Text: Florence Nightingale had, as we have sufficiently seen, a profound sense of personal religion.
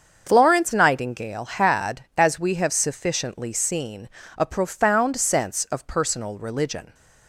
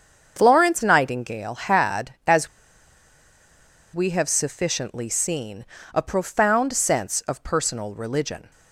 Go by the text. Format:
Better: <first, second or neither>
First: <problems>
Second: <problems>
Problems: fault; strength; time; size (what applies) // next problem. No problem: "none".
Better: first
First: starts louder than the rest; until 1.2 s; 7 dB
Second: starts louder than the rest; until 1.3 s; 7 dB // pauses between "as" and "we"; strong; at 2.4 s; 1.4 s long